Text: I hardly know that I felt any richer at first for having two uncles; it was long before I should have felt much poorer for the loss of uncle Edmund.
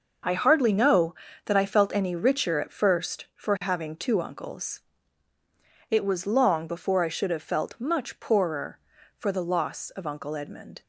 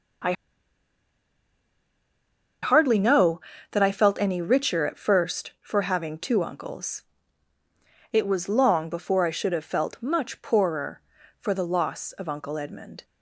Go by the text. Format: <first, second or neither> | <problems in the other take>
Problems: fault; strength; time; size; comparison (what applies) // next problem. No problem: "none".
first | starts louder than the rest; until 3.8 s; 6.5 dB; also in the first // pauses between "I" and "hardly"; strong; at 0.3 s; 2.3 s long